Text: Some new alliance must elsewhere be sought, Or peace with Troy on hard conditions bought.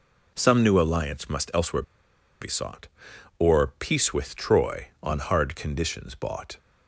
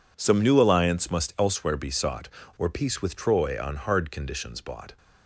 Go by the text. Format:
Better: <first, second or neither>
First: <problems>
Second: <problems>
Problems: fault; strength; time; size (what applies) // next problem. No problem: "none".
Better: second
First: pauses between "elsewhere" and "be"; noticeable; at 1.8 s; 0.57 s long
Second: none